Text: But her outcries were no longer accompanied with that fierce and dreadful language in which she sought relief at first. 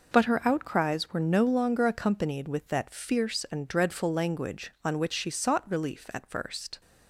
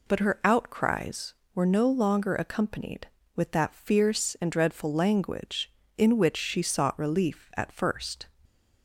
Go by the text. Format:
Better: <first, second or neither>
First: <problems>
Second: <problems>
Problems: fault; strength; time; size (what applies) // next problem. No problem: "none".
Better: second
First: says "on" for "in"; at 4.8 s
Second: none